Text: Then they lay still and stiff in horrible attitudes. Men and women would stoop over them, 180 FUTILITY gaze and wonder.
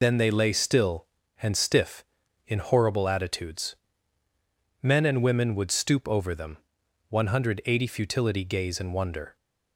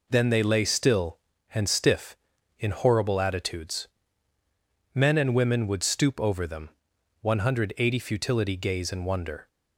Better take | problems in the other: second | loses the start of "Then"; at 0.0 s; 35 ms

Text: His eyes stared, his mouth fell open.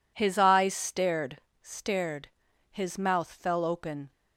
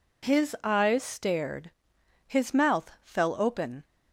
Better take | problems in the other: second | says "stared" twice; at 1.6 s

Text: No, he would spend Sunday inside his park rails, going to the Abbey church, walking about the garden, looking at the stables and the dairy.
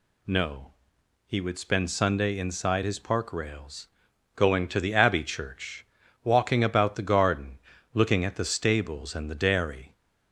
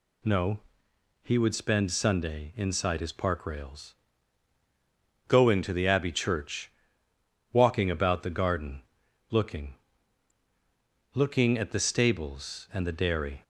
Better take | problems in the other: first | says "looking" twice; at 11.1 s

